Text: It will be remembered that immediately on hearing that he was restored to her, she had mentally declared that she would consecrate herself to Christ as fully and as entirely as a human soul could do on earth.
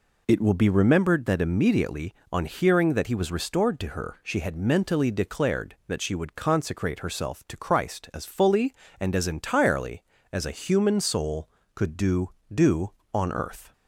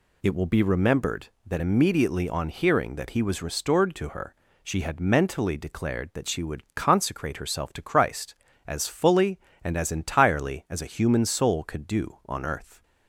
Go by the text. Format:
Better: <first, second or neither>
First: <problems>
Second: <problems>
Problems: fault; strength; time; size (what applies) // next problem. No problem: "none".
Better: second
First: says "do" twice; at 12.5 s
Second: none